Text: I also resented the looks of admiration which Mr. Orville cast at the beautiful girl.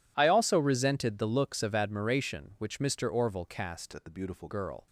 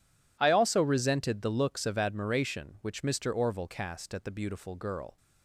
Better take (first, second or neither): second